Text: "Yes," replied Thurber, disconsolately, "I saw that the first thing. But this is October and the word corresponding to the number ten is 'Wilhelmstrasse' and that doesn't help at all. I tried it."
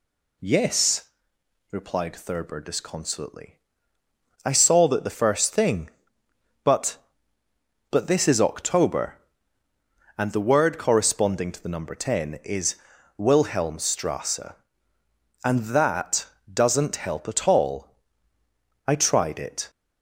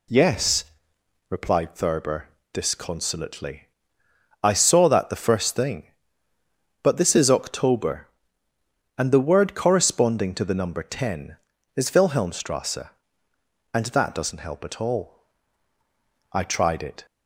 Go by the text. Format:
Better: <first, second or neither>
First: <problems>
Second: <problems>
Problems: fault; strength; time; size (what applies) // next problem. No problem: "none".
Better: second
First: says "But" twice; at 7.8 s // pauses between "is" and "Wilhelmstrasse"; at 12.7 s; 0.40 s long // pauses between "that" and "doesn't"; slight; at 16.2 s; 0.26 s long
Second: none